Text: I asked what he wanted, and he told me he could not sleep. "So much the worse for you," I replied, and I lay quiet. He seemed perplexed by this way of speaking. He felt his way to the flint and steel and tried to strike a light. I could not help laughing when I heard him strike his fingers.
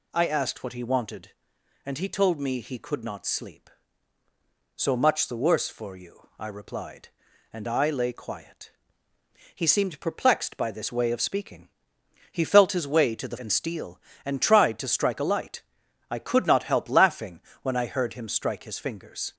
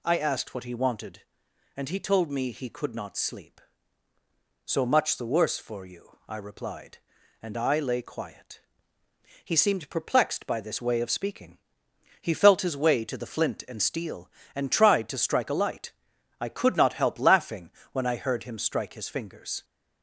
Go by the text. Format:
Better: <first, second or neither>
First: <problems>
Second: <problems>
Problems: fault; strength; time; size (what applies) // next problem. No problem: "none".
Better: second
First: skips "flint"; at 13.3 s // pauses between "laughing" and "when"; slight; at 17.4 s; 0.20 s long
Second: pauses between "laughing" and "when"; slight; at 17.7 s; 0.20 s long